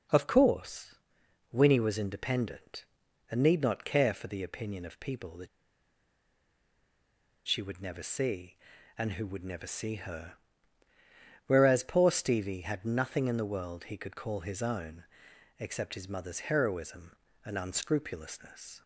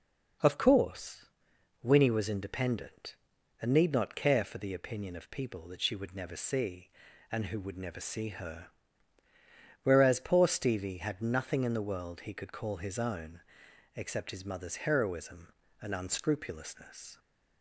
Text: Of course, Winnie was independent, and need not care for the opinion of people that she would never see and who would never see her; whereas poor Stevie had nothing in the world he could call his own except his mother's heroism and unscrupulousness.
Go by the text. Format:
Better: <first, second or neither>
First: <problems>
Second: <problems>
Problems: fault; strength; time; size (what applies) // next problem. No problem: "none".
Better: second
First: pauses between "that" and "she"; strong; at 5.4 s; 2.0 s long // pauses between "own" and "except"; noticeable; at 15.0 s; 0.54 s long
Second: pauses between "own" and "except"; noticeable; at 13.4 s; 0.54 s long